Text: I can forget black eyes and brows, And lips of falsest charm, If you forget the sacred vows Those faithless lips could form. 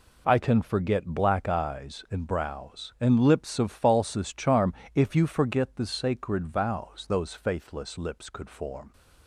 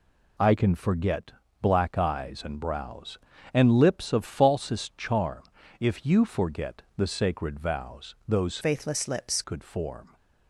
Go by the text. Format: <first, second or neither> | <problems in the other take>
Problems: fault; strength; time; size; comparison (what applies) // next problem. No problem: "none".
first | pauses between "forget" and "black"; slight; at 1.3 s; 0.32 s long // pauses between "vows" and "Those"; slight; at 8.1 s; 0.16 s long // changes voice from "faithless" to "lips"; from 8.6 to 9.4 s; 0.8 s long